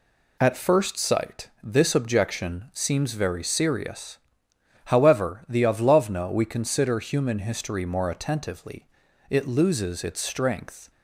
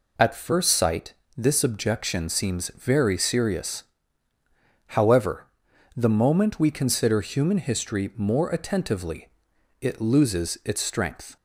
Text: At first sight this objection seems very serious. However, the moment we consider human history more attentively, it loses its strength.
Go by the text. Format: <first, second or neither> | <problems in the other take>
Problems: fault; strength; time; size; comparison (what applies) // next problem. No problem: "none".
second | pauses between "sight" and "this"; slight; at 1.4 s; 0.16 s long; slight in the second // says "avlovna" for "moment"; at 5.6 s